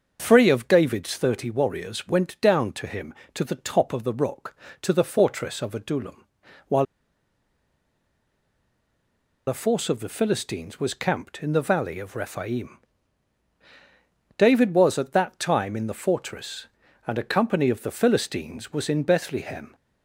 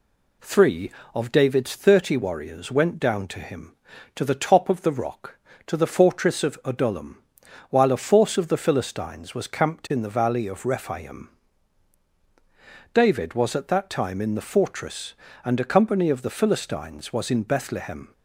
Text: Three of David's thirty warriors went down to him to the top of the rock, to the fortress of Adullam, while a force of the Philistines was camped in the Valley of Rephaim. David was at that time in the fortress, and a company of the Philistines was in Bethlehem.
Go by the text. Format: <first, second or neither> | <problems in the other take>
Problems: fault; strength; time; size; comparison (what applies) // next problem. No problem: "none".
second | starts louder than the rest; until 1.2 s; 6.5 dB // pauses between "while" and "a"; strong; at 6.8 s; 2.6 s long